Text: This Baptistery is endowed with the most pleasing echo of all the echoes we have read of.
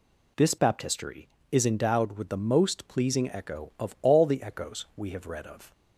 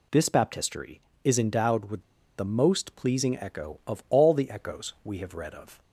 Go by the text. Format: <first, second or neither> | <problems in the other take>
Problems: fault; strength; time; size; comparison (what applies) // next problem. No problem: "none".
first | pauses between "with" and "the"; at 2.0 s; 0.37 s long